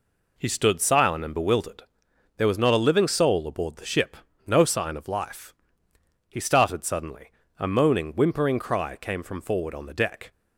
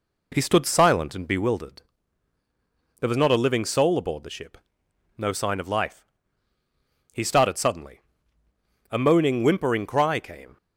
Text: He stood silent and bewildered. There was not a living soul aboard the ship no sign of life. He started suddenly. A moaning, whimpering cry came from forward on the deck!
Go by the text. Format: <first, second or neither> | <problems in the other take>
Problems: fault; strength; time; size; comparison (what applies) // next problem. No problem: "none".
first | pauses between "ship" and "no"; noticeable; at 4.5 s; 0.58 s long; slight in the first // stops before "from forward on the deck"; at 10.5 s